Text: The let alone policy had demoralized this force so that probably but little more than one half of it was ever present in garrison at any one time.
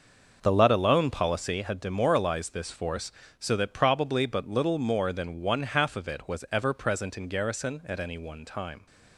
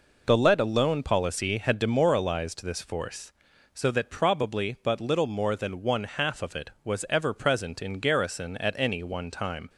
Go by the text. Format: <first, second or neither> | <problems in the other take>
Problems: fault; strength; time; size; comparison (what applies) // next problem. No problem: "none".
second | starts louder than the rest; until 1.5 s; 6 dB